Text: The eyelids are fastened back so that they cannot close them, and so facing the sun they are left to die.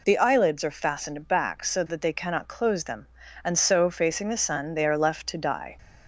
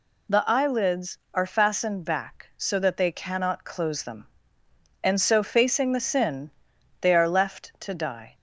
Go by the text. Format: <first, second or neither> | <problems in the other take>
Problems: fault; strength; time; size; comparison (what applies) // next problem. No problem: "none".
first | says "sin" for "sun"; at 6.0 s